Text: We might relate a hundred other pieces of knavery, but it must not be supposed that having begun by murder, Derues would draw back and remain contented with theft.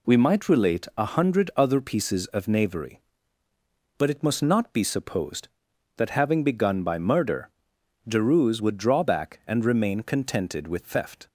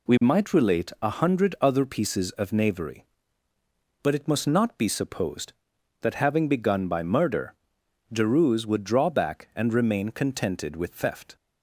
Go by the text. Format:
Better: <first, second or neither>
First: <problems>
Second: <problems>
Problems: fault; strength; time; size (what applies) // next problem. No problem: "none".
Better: neither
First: none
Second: none